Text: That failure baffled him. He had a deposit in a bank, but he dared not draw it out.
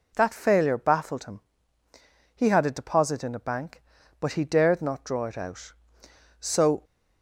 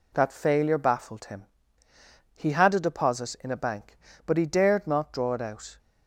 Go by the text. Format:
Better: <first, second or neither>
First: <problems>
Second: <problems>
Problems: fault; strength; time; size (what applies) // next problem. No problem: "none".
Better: second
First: goes on to say "So"; slight; from 6.3 s on; 0.44 s long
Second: none